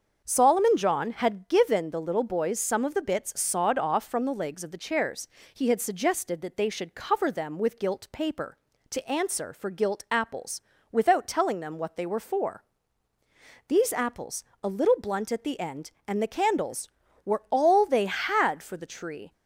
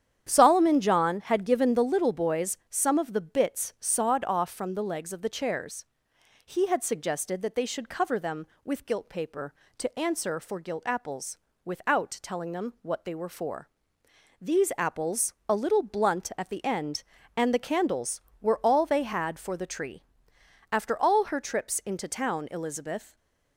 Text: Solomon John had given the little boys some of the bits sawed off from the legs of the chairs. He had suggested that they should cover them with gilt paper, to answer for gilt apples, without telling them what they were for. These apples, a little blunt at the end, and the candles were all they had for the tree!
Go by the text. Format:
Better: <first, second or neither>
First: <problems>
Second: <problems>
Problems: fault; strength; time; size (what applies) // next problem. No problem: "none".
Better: first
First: starts louder than the rest; until 1.2 s; 6.5 dB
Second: starts louder than the rest; strong; until 1.3 s; 9 dB // goes on to say "After all her trips into town Elizabeth"; strong; from 20.7 s on; 2.4 s long // stays silent after the last word; slight; from 23.0 s on; 0.5 s long